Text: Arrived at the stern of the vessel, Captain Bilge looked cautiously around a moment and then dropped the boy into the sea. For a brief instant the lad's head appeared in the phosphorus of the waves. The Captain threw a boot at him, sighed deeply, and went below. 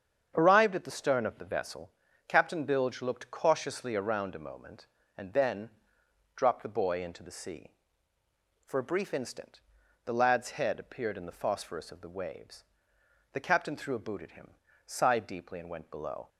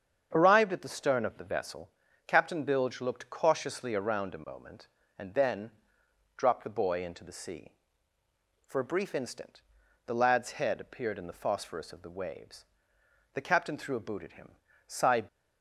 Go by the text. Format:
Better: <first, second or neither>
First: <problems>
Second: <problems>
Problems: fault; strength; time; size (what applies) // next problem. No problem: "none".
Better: first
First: starts louder than the rest; strong; until 1.3 s; 7.5 dB // pauses between "then" and "dropped"; noticeable; at 5.6 s; 0.66 s long // pauses between "instant" and "the"; noticeable; at 9.6 s; 0.46 s long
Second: starts louder than the rest; strong; until 1.3 s; 7.5 dB // pauses between "then" and "dropped"; noticeable; at 5.6 s; 0.66 s long // pauses between "instant" and "the"; noticeable; at 9.6 s; 0.46 s long // stops before "deeply and went below"; at 15.2 s